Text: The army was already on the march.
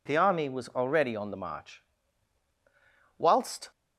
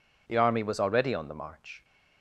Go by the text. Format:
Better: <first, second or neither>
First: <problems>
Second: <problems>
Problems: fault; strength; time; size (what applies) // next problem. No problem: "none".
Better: second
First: goes on to say "Whilst"; from 3.1 s on; 0.52 s long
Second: none